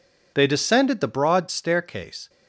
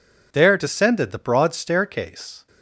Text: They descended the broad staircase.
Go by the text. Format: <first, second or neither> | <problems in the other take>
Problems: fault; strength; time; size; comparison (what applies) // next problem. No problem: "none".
first | says "There" for "They"; at 0.3 s